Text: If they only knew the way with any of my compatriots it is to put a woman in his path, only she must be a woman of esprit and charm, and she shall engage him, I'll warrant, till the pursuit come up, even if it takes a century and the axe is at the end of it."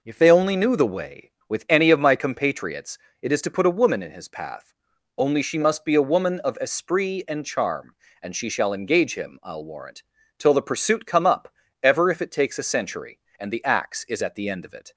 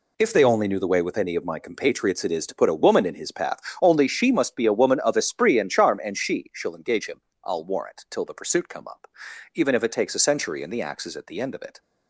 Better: second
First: pauses between "compatriots" and "it"; slight; at 2.9 s; 0.24 s long // says "ever" for "even"; at 11.8 s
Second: none

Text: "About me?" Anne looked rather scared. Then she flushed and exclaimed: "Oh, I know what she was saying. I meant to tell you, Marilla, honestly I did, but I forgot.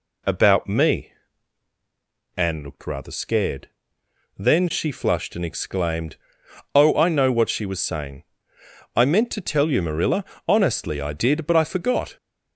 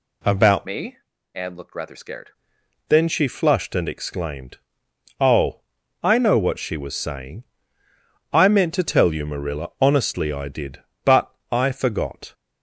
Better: first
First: none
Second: changes voice from "me" to "scared"; from 0.6 to 2.3 s; 1.7 s long // pauses between "but" and "I"; slight; at 11.3 s; 0.16 s long

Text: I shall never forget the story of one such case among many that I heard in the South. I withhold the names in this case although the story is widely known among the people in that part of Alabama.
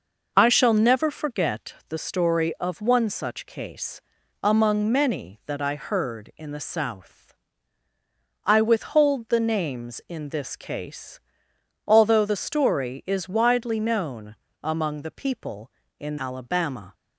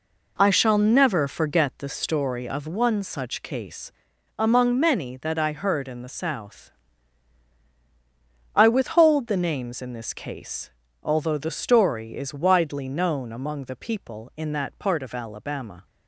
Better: second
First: pauses between "forget" and "the"; slight; at 1.7 s; 0.16 s long // pauses between "case" and "among"; at 4.0 s; 0.40 s long // pauses between "case" and "although"; noticeable; at 11.1 s; 0.66 s long // pauses between "known" and "among"; slight; at 14.3 s; 0.30 s long // skips "that part of"; at 16.1 s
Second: pauses between "case" and "among"; noticeable; at 3.9 s; 0.46 s long // pauses between "case" and "although"; slight; at 10.7 s; 0.30 s long

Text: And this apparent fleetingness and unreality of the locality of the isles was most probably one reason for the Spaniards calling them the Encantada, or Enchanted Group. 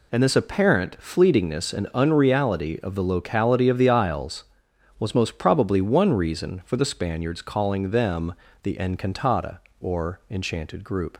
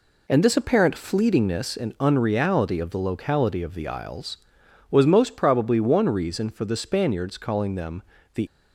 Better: first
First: pauses between "them" and "the"; slight; at 8.3 s; 0.30 s long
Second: pauses between "them" and "the"; slight; at 8.0 s; 0.32 s long // stops before "Encantada or Enchanted Group"; at 8.4 s

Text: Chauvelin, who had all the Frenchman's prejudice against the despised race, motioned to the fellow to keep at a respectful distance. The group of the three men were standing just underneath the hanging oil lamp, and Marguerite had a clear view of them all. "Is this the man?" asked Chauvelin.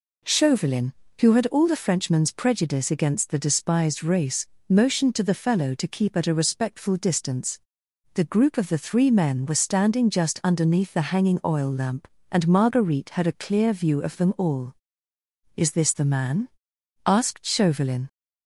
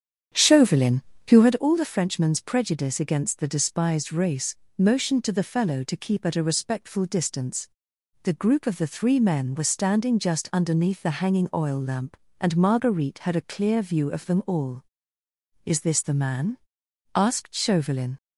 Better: first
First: none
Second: starts louder than the rest; strong; until 1.7 s; 8.5 dB

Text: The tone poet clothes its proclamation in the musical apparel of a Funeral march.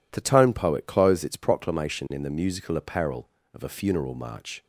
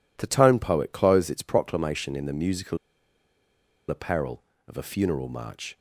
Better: first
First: none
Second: pauses between "musical" and "apparel"; at 2.7 s; 1.1 s long

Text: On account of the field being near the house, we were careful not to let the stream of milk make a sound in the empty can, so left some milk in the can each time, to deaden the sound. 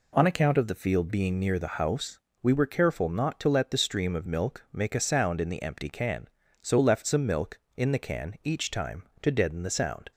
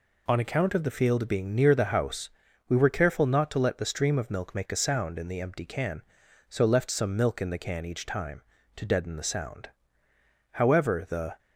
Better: first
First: none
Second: goes on to say "However the"; noticeable; from 10.5 s on; 0.86 s long

